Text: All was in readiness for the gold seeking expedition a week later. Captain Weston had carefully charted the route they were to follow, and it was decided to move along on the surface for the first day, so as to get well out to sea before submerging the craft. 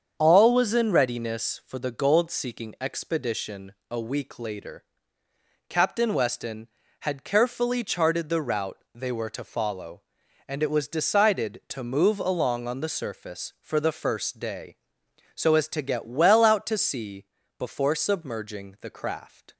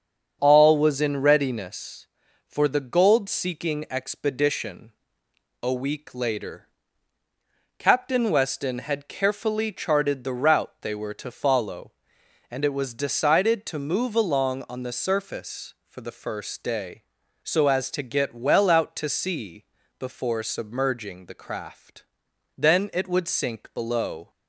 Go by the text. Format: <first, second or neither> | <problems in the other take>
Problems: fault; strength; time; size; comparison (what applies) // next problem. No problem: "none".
first | starts louder than the rest; until 1.4 s; 7 dB; strong in the first // pauses between "expedition" and "a"; noticeable; at 4.9 s; 0.70 s long; slight in the first // pauses between "sea" and "before"; slight; at 19.6 s; 0.34 s long; slight in the first // goes on to say "Then it would sink below"; strong; from 22.5 s on; 1.7 s long